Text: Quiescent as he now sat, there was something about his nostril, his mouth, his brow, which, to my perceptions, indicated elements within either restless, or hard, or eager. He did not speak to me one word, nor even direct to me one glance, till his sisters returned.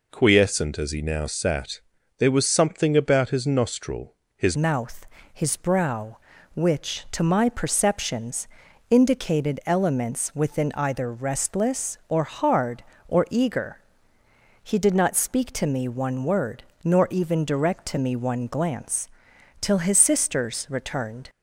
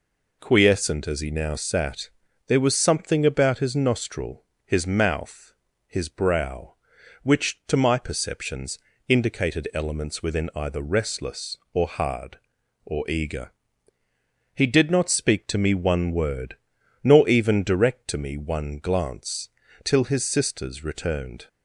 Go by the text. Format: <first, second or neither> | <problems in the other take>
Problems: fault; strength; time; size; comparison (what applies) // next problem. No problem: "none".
second | changes voice at "mouth"; from 4.5 s on; 16.7 s long